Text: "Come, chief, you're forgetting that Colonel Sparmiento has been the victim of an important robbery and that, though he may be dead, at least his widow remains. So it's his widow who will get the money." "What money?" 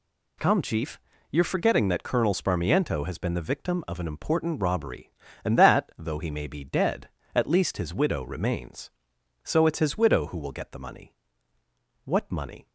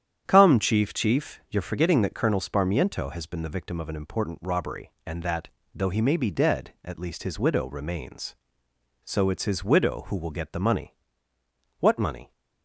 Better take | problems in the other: first | starts louder than the rest; strong; until 1.2 s; 9.5 dB // says "chief" twice; at 0.9 s

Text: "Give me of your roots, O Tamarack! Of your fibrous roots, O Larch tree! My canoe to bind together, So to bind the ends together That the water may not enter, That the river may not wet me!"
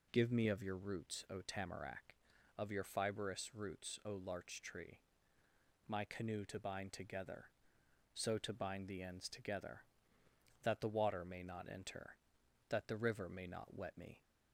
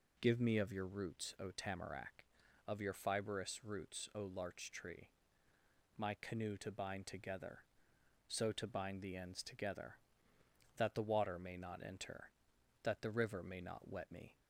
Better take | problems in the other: neither | none

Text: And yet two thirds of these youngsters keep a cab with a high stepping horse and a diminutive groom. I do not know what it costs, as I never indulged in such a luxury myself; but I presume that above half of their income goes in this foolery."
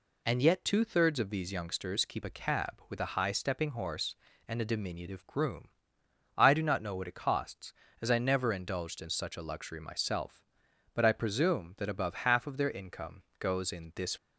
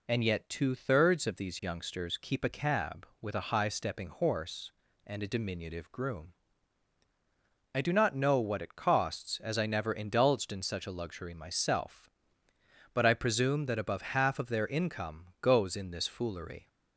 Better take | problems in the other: second | pauses between "income" and "goes"; slight; at 13.2 s; 0.16 s long // stops before "foolery"; at 14.1 s

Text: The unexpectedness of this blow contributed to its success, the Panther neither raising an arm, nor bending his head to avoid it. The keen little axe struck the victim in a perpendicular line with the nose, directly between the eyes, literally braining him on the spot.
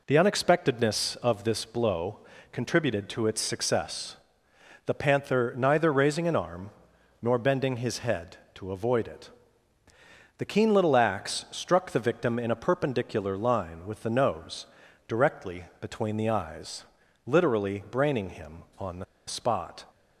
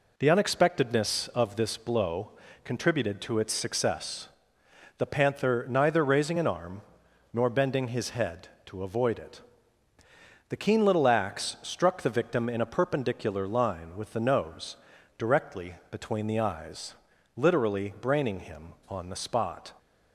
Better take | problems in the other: second | pauses between "blow" and "contributed"; slight; at 2.1 s; 0.32 s long; slight in the second // pauses between "directly" and "between"; slight; at 15.6 s; 0.16 s long; slight in the second // pauses between "the" and "spot"; slight; at 19.0 s; 0.23 s long

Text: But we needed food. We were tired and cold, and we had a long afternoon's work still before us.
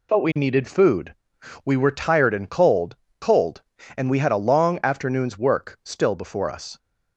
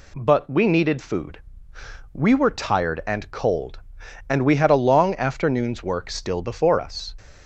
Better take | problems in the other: second | says "cold" twice; at 3.1 s

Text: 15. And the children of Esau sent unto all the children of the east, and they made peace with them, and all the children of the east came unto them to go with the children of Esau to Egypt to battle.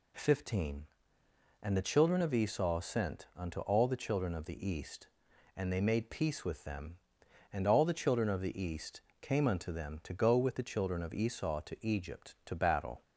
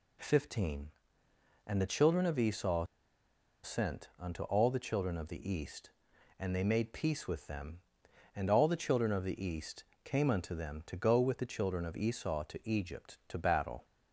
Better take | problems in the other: first | pauses between "Esau" and "sent"; noticeable; at 2.8 s; 0.79 s long // pauses between "east" and "came"; slight; at 9.8 s; 0.22 s long; slight in the first

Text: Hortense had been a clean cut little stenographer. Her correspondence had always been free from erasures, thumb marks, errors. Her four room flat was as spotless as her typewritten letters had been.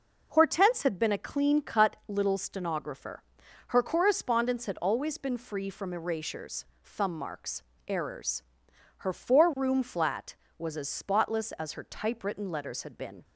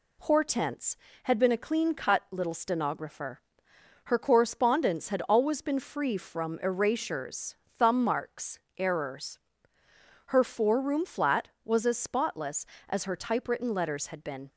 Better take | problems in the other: neither | none

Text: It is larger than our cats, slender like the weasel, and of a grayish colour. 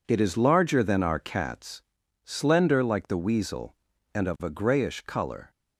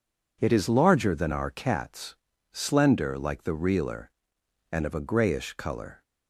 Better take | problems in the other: first | says "reeler" for "weasel"; at 3.5 s

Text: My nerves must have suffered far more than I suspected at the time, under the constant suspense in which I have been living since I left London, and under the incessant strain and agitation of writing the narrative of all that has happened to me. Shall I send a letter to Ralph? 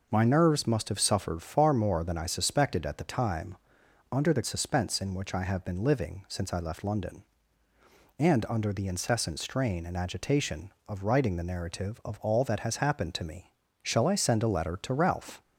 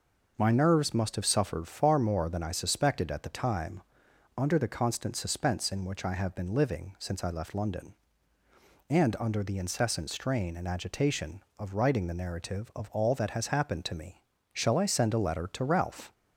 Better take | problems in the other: second | skips "constant"; at 4.4 s

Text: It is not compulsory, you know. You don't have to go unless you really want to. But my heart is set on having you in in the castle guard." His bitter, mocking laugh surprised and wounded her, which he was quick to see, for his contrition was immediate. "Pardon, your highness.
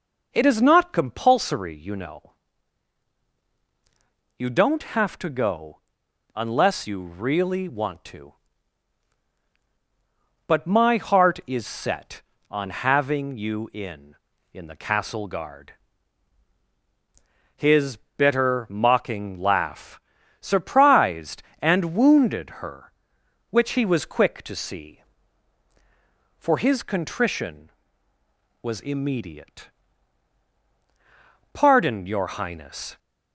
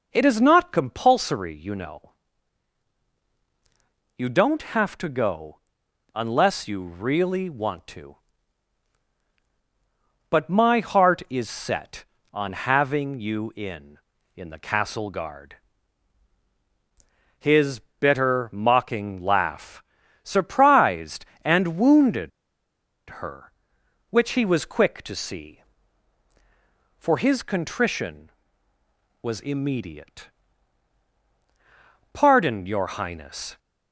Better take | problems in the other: first | pauses between "go" and "unless"; noticeable; at 5.5 s; 0.54 s long; noticeable in the first // pauses between "His" and "bitter"; slight; at 17.8 s; 0.20 s long; slight in the first // pauses between "laugh" and "surprised"; at 19.8 s; 0.40 s long; also in the first // pauses between "wounded" and "her"; noticeable; at 22.3 s; 0.89 s long

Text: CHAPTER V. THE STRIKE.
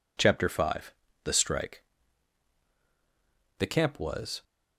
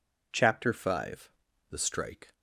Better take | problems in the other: second | goes on to say "THE camp was"; noticeable; from 3.5 s on; 0.84 s long

